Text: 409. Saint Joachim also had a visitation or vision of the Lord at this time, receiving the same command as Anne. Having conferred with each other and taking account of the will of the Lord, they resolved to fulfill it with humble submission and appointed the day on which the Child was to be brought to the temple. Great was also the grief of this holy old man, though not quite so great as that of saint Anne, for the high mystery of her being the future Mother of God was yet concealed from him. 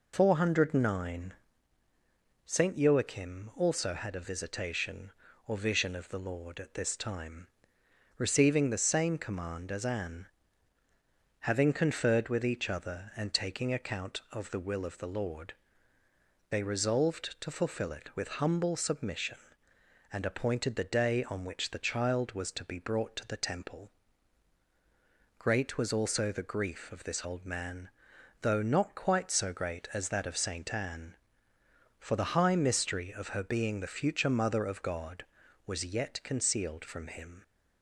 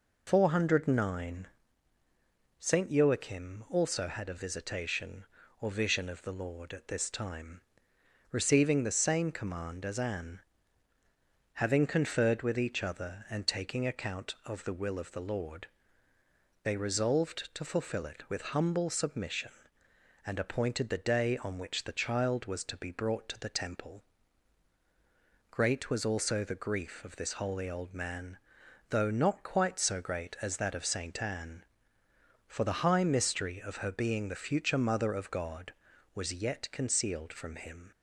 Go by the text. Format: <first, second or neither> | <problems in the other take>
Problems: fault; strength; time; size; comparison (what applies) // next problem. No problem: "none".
second | skips "holy"; at 27.2 s